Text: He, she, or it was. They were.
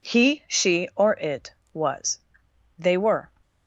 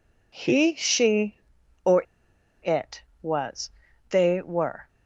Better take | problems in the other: first | pauses between "or" and "it"; noticeable; at 2.0 s; 0.60 s long

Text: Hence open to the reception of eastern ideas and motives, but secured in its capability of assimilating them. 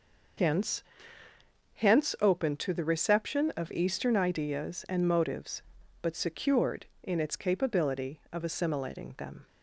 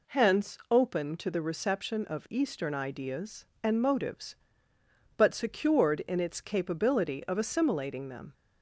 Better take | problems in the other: second | says "Hence" twice; at 1.7 s

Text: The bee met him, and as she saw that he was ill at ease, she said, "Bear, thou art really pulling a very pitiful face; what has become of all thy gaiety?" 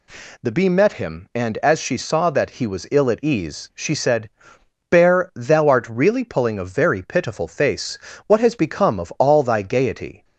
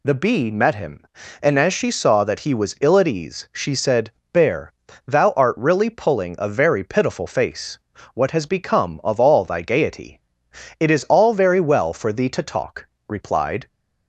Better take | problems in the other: first | goes on to say "It is all very well for thee to talk replied"; strong; from 10.7 s on; 2.8 s long

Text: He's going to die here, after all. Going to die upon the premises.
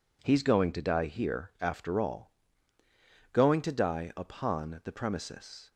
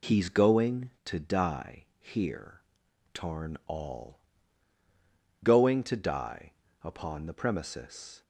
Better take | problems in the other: first | says "tarn" for "after"; at 3.1 s // pauses between "die" and "upon"; slight; at 6.5 s; 0.30 s long

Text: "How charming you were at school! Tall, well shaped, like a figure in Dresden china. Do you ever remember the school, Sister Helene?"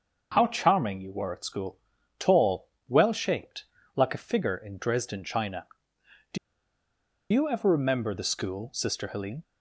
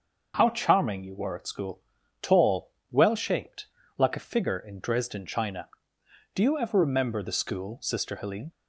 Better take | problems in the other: second | starts louder than the rest; until 1.3 s; 6.5 dB; also in the second // pauses between "Do" and "you"; noticeable; at 6.3 s; 0.95 s long

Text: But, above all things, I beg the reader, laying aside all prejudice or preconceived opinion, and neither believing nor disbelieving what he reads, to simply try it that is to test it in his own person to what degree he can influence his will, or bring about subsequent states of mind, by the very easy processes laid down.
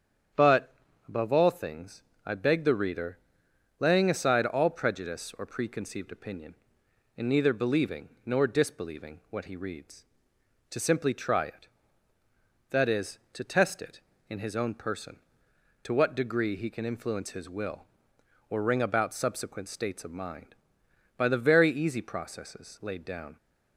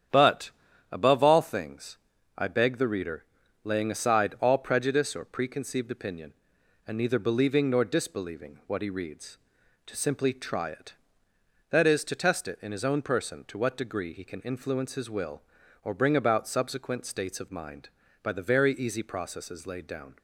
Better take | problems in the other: second | starts louder than the rest; strong; until 1.6 s; 8 dB; strong in the second // pauses between "believing" and "nor"; slight; at 8.0 s; 0.16 s long // says "ring" for "bring"; at 18.6 s

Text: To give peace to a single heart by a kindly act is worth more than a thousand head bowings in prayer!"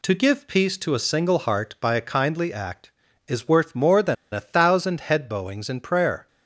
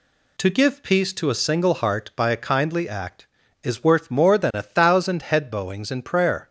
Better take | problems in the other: second | pauses between "than" and "a"; slight; at 4.1 s; 0.17 s long

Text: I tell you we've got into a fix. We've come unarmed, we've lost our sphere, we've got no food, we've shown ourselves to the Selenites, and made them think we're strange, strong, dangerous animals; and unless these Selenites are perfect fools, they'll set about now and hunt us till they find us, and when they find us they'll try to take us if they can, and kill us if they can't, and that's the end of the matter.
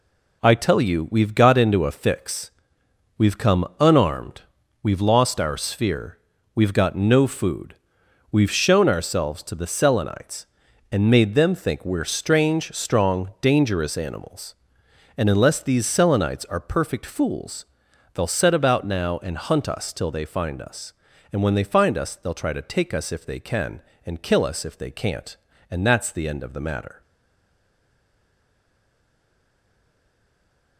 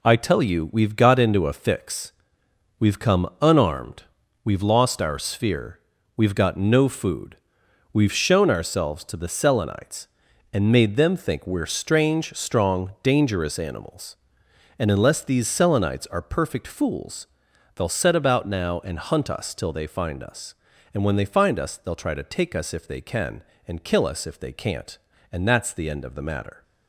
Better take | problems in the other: second | stays silent after the last word; strong; from 27.0 s on; 3.7 s long

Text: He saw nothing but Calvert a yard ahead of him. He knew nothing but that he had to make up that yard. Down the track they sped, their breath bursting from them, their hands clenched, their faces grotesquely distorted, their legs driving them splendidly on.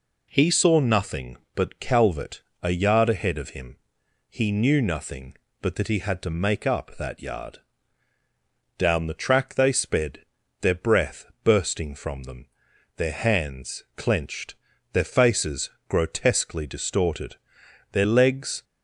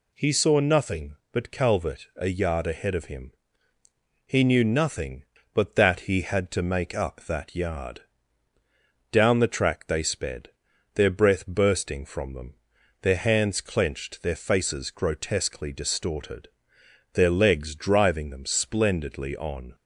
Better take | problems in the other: second | pauses between "Calvert" and "a"; slight; at 2.4 s; 0.18 s long // pauses between "breath" and "bursting"; slight; at 11.2 s; 0.18 s long // pauses between "faces" and "grotesquely"; slight; at 15.7 s; 0.16 s long // stops before "driving them splendidly on"; at 18.6 s

